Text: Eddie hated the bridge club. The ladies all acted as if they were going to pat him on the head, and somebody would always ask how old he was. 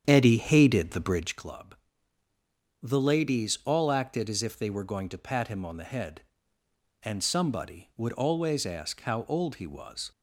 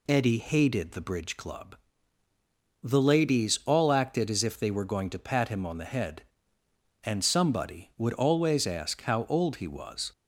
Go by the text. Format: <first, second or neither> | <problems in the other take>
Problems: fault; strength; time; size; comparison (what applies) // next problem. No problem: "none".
second | starts louder than the rest; strong; until 1.4 s; 8.5 dB